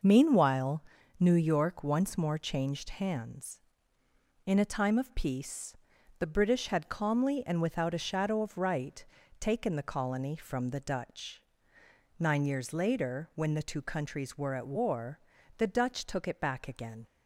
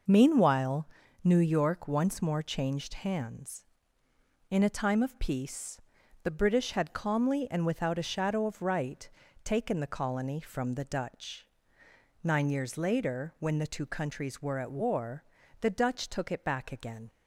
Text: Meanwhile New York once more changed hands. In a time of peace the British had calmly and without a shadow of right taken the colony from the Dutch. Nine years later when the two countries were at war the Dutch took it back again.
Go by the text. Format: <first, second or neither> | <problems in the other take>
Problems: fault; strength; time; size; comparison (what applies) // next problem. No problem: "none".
neither | pauses between "Meanwhile" and "New"; slight; the same in both // pauses between "peace" and "the"; the same in both // pauses between "right" and "taken"; slight; the same in both // pauses between "war" and "the"; the same in both